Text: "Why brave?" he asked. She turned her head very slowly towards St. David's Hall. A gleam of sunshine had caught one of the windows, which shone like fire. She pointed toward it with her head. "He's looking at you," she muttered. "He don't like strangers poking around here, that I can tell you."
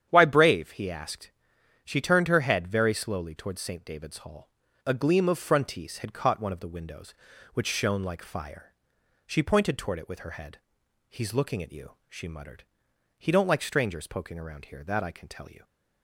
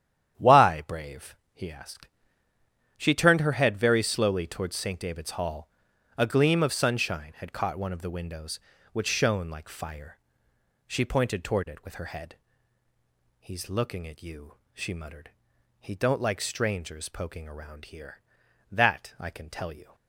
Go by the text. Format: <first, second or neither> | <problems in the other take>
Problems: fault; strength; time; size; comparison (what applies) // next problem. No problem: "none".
second | starts louder than the rest; strong; until 1.1 s; 9 dB; strong in the second // says "frontise" for "sunshine"; at 5.3 s